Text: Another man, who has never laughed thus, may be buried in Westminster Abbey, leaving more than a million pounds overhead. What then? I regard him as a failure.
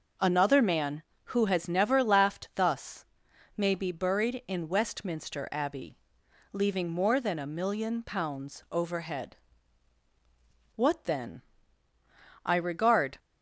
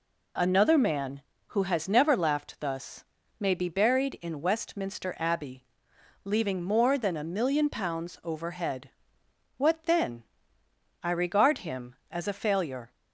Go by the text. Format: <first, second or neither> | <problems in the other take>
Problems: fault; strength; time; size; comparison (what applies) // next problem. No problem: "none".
second | stops before "him as a failure"; at 13.1 s